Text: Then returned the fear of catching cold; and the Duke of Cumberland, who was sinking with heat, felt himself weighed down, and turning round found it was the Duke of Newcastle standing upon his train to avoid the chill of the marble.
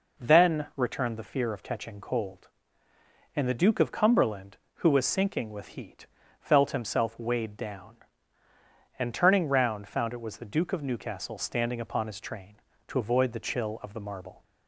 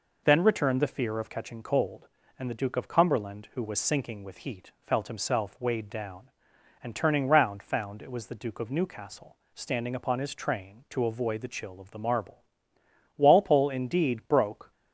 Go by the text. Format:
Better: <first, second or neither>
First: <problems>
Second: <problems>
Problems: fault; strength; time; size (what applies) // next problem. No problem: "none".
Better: first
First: none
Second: pauses between "Newcastle" and "standing"; slight; at 9.3 s; 0.18 s long // goes on to say "Walpole indeed broke"; from 13.1 s on; 1.5 s long